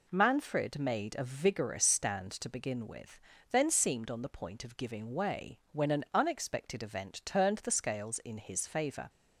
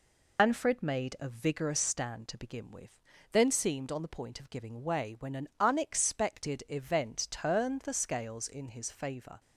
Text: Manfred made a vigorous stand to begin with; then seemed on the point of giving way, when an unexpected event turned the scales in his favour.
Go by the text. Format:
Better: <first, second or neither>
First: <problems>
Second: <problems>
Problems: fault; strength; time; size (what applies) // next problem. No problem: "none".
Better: first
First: none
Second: loses the start of "Manfred"; at 0.3 s; 120 ms